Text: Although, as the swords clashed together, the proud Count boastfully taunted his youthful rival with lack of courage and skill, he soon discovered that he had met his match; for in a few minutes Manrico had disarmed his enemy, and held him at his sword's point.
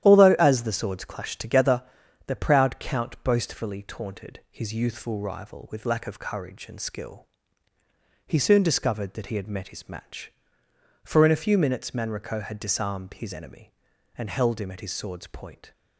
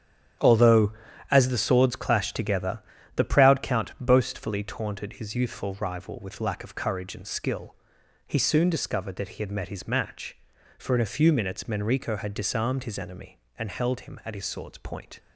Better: neither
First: starts louder than the rest; strong; until 1.0 s; 11.5 dB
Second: starts louder than the rest; strong; until 1.8 s; 10 dB

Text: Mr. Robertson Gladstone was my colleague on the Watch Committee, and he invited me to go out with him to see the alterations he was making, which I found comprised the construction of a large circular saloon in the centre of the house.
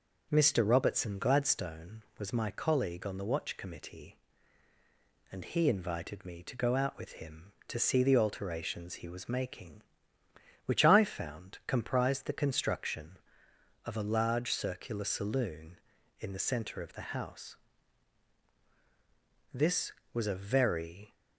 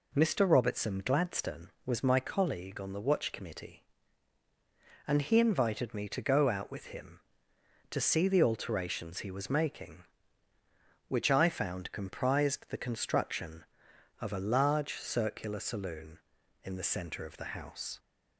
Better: second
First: goes on to say "This was a very"; from 19.5 s on; 1.6 s long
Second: none

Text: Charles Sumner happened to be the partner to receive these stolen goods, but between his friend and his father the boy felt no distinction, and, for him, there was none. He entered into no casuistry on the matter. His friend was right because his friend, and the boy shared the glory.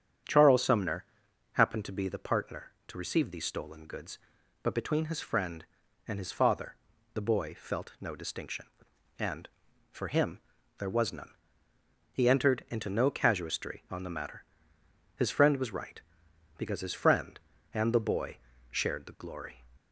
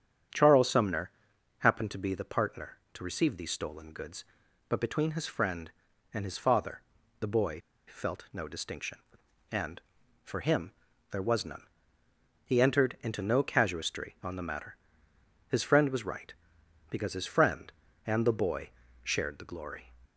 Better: first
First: starts louder than the rest; strong; until 1.7 s; 8 dB // pauses between "Sumner" and "happened"; noticeable; at 1.0 s; 0.48 s long // pauses between "father" and "the"; at 6.7 s; 0.38 s long // pauses between "boy" and "shared"; slight; at 18.3 s; 0.32 s long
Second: starts louder than the rest; strong; until 1.8 s; 8 dB // pauses between "Sumner" and "happened"; noticeable; at 1.1 s; 0.48 s long // pauses between "father" and "the"; at 6.8 s; 0.38 s long // pauses between "boy" and "felt"; slight; at 7.6 s; 0.28 s long // pauses between "boy" and "shared"; slight; at 18.7 s; 0.32 s long

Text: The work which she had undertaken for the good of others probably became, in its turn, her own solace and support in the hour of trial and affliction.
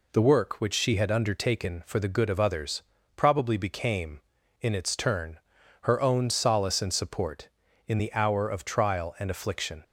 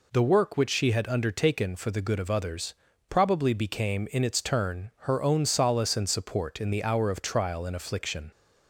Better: neither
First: pauses between "others" and "probably"; slight; at 2.8 s; 0.34 s long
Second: pauses between "others" and "probably"; slight; at 2.7 s; 0.36 s long

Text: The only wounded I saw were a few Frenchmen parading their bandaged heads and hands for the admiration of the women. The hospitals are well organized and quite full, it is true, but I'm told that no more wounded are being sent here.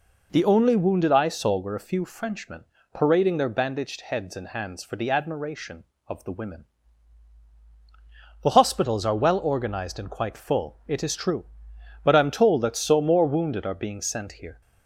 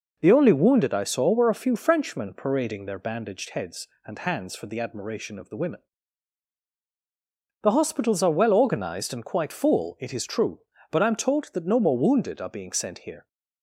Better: second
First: pauses between "Frenchmen" and "parading"; slight; at 2.6 s; 0.30 s long // says "so" for "no"; at 12.7 s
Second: none

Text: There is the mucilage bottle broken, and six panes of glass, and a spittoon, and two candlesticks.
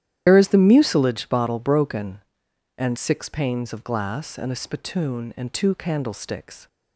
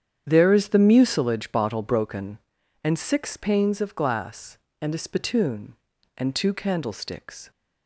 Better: second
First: loses the start of "There"; at 0.2 s; 95 ms // starts louder than the rest; strong; until 1.2 s; 11.5 dB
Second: starts louder than the rest; strong; until 1.2 s; 8.5 dB

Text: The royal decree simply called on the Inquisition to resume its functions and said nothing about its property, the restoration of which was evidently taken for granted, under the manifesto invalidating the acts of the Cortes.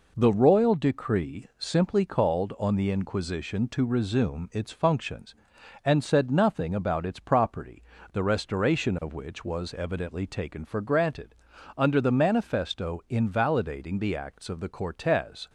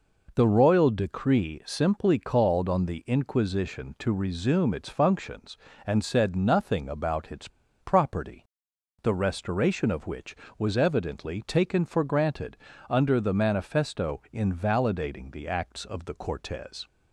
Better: first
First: none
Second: pauses between "its" and "property"; slight; at 7.4 s; 0.32 s long

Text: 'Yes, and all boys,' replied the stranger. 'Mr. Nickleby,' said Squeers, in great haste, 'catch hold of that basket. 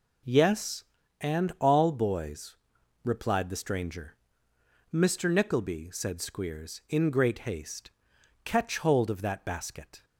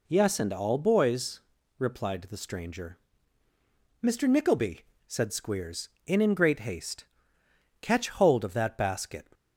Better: first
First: none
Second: says "in" twice; at 6.2 s

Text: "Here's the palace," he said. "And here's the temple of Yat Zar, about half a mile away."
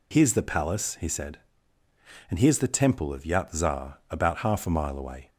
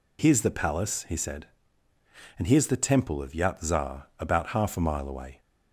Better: neither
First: none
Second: none

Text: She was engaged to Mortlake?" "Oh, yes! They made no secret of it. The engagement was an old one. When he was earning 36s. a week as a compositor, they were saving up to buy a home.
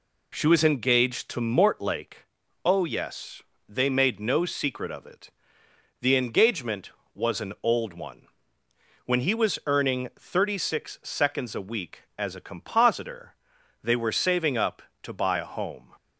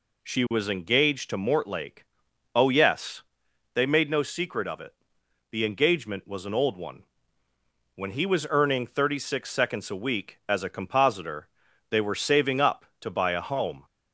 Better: neither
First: none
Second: none

